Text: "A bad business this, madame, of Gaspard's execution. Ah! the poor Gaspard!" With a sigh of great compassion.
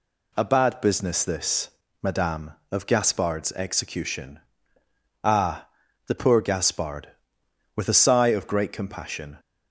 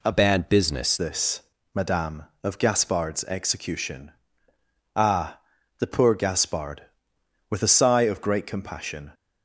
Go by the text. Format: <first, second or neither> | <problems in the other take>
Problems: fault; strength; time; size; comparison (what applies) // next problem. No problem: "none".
first | changes voice from "bad" to "business"; from 0.1 to 0.9 s; 0.8 s long